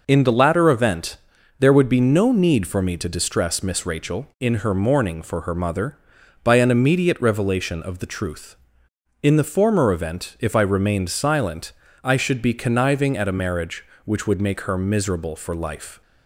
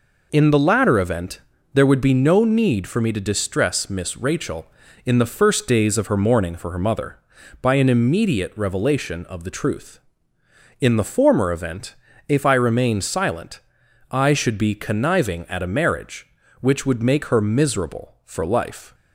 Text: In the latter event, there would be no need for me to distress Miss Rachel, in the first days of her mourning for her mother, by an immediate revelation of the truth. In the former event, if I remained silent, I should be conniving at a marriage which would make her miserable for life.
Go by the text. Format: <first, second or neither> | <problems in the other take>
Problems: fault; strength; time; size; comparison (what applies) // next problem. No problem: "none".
second | skips "the first days of"; at 4.5 s